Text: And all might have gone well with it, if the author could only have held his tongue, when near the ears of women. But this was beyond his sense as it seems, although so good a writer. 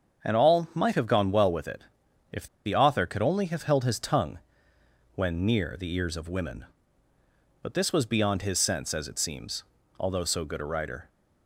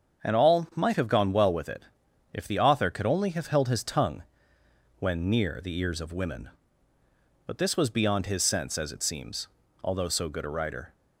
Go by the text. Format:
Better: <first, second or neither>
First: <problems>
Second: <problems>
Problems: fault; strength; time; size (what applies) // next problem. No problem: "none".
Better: second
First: starts louder than the rest; strong; until 1.3 s; 7 dB // pauses between "if" and "the"; slight; at 2.4 s; 0.20 s long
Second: starts louder than the rest; until 1.3 s; 7 dB